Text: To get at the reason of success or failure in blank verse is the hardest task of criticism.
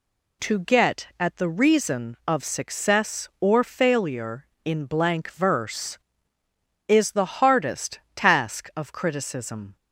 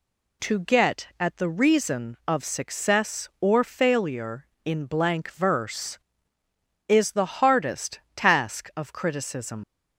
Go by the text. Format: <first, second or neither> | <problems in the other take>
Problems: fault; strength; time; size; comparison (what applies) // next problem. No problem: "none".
first | pauses between "hardest" and "task"; slight; at 7.9 s; 0.16 s long; slight in the first // leaves "criticism" unfinished; at 9.6 s; 120 ms